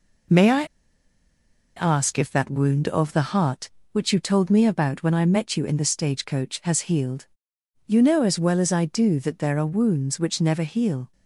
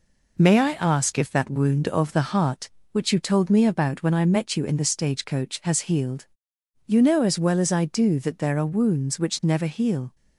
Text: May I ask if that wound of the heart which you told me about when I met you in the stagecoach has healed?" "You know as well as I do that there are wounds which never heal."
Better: second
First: pauses between "I" and "ask"; at 0.6 s; 1.1 s long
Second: none

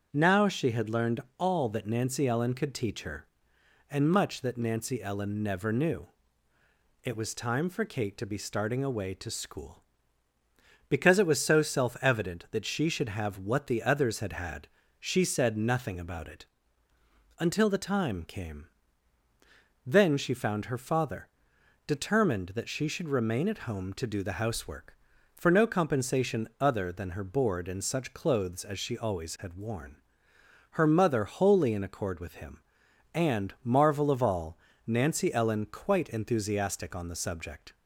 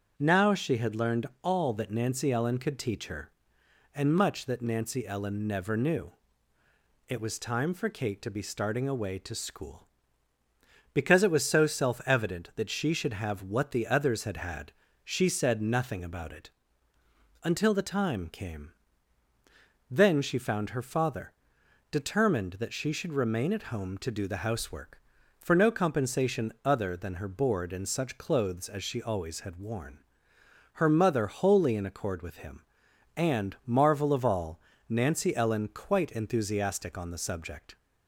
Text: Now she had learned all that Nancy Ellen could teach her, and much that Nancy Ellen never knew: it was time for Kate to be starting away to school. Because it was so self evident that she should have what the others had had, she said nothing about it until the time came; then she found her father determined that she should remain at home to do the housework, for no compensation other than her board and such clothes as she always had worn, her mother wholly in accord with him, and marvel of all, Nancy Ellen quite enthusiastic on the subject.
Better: neither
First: starts louder than the rest; strong; until 1.1 s; 7 dB // pauses between "learned" and "all"; slight; at 1.2 s; 0.18 s long // pauses between "it" and "until"; noticeable; at 16.4 s; 0.92 s long // pauses between "father" and "determined"; noticeable; at 21.2 s; 0.58 s long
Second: starts louder than the rest; strong; until 1.1 s; 7 dB // pauses between "learned" and "all"; slight; at 1.2 s; 0.16 s long // pauses between "it" and "until"; noticeable; at 16.5 s; 0.92 s long // pauses between "father" and "determined"; noticeable; at 21.3 s; 0.58 s long

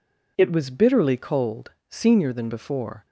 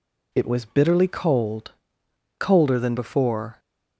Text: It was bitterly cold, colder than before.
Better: second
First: says "senior" for "colder"; at 1.8 s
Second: none

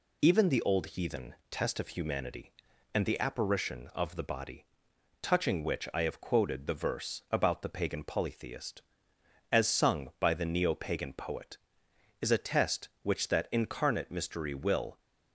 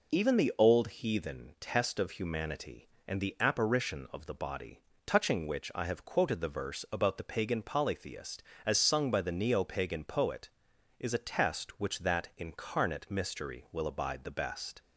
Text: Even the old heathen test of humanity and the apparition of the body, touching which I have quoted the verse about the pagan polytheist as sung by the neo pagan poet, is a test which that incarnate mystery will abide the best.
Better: second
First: pauses between "heathen" and "test"; slight; at 1.3 s; 0.16 s long // stops before "abide the best"; at 14.9 s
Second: none

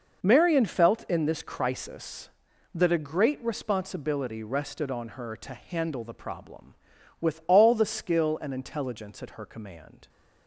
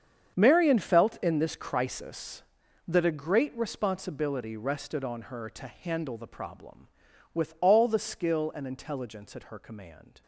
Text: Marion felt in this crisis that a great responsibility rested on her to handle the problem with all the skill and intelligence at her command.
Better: first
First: none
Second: gets quieter; strong; throughout; 14.5 dB

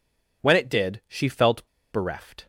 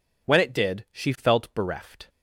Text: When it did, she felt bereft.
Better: second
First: pauses between "felt" and "bereft"; slight; at 1.6 s; 0.25 s long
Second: none

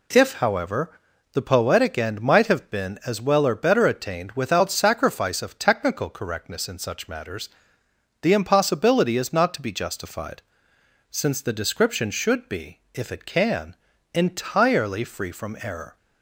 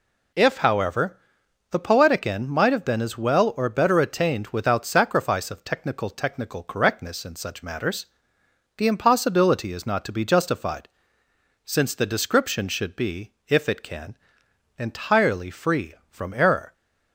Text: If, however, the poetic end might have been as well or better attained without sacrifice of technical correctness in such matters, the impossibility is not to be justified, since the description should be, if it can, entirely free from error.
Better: first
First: none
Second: says "technical" twice; at 6.0 s

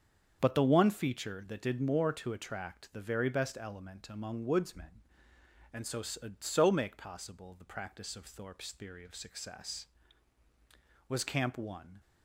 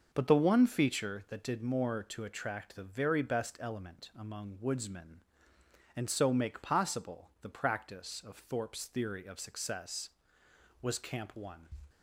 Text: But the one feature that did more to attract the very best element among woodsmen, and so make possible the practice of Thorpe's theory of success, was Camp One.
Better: second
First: starts louder than the rest; strong; until 1.4 s; 7.5 dB // says "so" twice; at 6.0 s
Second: starts louder than the rest; noticeable; until 1.1 s; 6 dB

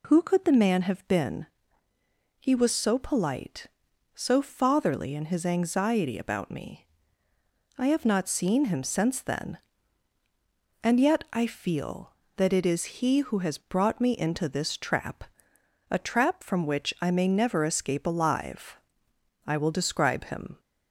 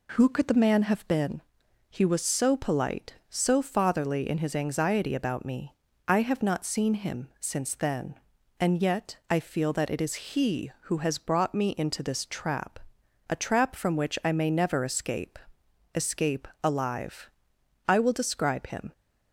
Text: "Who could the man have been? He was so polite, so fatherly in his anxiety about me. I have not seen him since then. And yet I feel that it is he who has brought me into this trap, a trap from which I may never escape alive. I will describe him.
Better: first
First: none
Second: says "escape" twice; at 15.9 s

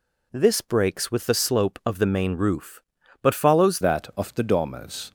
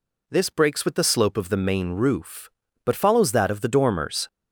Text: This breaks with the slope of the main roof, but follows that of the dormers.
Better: second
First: changes voice at "that"; from 3.8 s on; 1.3 s long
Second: none

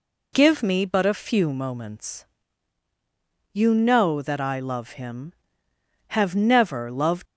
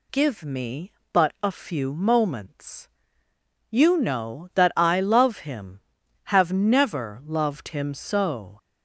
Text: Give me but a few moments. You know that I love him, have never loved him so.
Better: second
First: stops before "him so"; at 7.2 s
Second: none

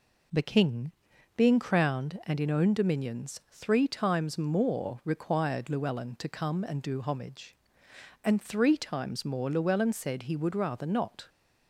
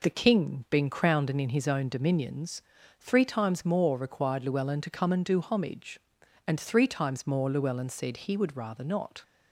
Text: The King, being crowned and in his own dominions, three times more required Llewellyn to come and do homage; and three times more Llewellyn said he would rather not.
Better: second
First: skips "his"; at 2.5 s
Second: none

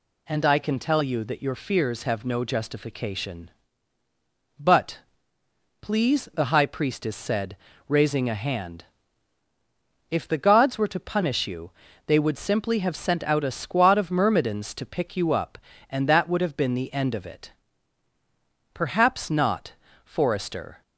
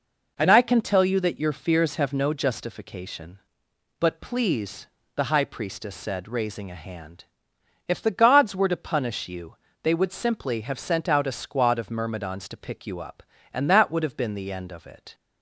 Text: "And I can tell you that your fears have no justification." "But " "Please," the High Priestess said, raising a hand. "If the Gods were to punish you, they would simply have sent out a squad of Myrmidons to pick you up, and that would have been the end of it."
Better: second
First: goes on to say "Perhaps not Forrester"; strong; from 18.7 s on; 2.0 s long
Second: none

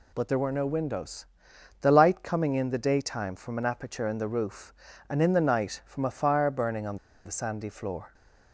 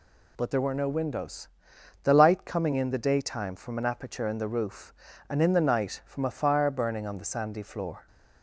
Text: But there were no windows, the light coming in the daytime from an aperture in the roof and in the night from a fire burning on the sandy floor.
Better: second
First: pauses between "on" and "the"; slight; at 6.9 s; 0.27 s long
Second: none

